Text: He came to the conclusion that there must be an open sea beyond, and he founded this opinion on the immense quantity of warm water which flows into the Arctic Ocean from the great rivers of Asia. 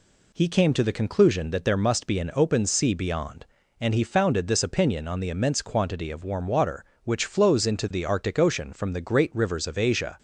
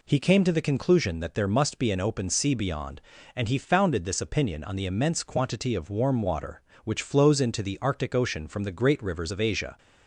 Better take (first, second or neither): neither